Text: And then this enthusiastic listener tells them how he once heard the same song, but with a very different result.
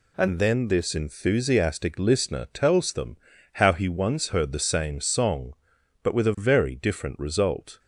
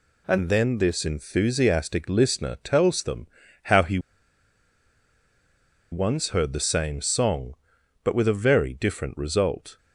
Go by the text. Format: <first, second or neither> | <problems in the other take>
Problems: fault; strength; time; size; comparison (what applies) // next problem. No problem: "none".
first | pauses between "them" and "how"; at 3.2 s; 0.38 s long; also in the first // pauses between "he" and "once"; strong; at 3.9 s; 1.9 s long